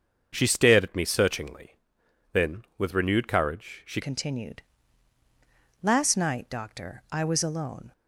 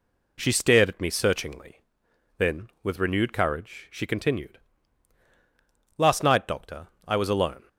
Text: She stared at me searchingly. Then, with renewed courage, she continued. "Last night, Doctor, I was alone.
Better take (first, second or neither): second